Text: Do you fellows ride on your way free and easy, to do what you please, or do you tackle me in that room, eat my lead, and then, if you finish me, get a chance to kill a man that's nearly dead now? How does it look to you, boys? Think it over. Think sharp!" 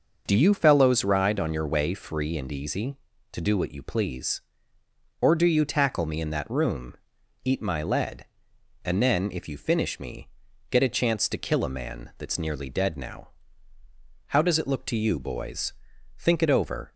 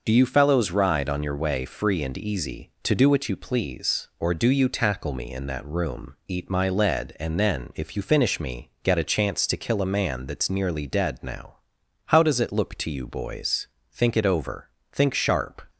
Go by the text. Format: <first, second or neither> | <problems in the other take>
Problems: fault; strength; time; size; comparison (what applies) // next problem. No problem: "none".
second | stops before "Think sharp"; at 16.9 s